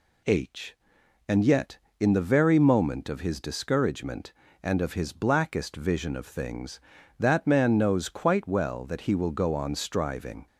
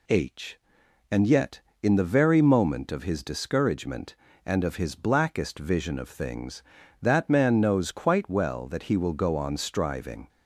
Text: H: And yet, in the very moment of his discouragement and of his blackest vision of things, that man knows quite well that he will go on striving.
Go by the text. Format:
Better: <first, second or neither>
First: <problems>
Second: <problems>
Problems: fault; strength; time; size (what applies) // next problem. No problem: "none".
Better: neither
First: none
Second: none